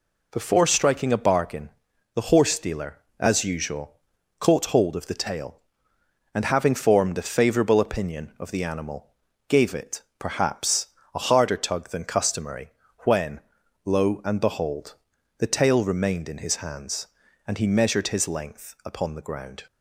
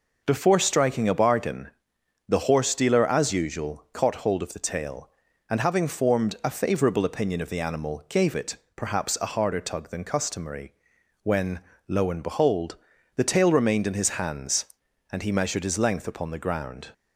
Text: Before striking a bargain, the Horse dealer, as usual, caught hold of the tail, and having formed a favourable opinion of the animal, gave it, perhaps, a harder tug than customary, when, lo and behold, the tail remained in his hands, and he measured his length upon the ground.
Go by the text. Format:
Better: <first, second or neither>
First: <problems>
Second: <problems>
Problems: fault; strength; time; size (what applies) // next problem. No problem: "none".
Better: neither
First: none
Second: none